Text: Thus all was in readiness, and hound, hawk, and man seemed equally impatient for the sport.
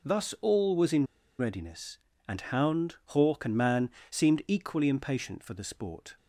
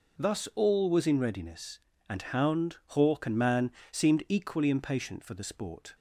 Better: second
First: pauses between "in" and "readiness"; slight; at 1.0 s; 0.32 s long // pauses between "man" and "seemed"; slight; at 3.8 s; 0.22 s long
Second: pauses between "man" and "seemed"; slight; at 3.6 s; 0.22 s long

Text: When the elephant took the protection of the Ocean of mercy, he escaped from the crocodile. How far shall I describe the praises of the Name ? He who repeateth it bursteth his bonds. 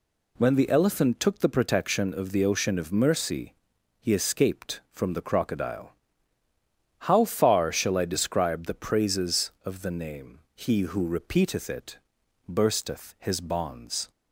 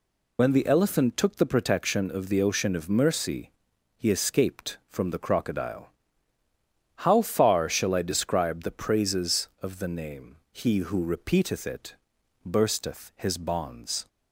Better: first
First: pauses between "it" and "bursteth"; noticeable; at 11.9 s; 0.50 s long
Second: loses the start of "When"; at 0.3 s; 70 ms // pauses between "it" and "bursteth"; noticeable; at 11.9 s; 0.50 s long

